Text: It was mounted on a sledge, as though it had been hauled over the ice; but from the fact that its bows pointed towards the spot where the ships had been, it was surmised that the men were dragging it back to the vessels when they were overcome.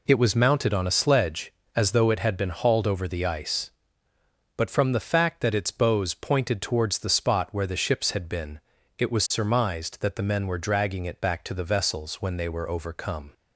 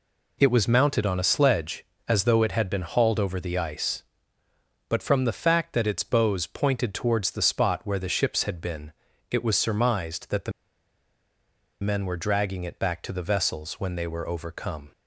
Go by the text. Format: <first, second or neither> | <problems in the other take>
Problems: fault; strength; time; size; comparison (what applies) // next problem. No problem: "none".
first | pauses between "the" and "men"; strong; at 10.5 s; 1.2 s long